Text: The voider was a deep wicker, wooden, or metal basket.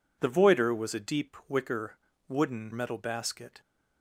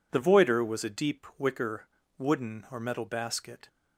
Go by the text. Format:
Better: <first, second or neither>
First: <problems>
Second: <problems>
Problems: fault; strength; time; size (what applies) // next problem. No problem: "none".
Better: second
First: skips "or"; at 2.7 s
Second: none